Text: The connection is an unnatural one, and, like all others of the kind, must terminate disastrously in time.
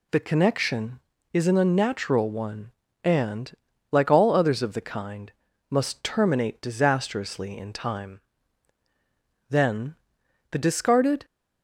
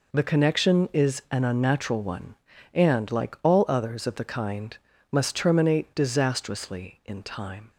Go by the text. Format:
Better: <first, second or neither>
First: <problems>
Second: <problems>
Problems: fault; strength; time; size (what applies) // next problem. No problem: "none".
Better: second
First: goes on to say "Then the discarded"; strong; from 9.4 s on; 1.7 s long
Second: none